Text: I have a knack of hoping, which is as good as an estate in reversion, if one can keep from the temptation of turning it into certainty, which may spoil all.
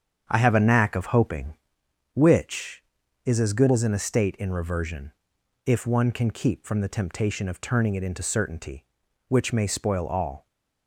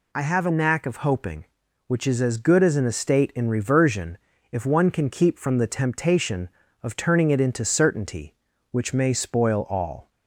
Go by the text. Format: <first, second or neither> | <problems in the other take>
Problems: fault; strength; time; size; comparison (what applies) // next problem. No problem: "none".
second | starts louder than the rest; strong; until 1.8 s; 8 dB